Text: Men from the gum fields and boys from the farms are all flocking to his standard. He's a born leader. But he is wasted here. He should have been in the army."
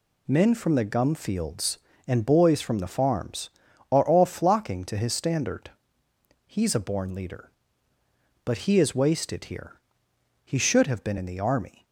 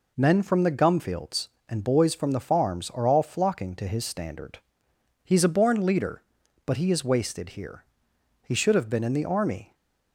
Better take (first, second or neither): neither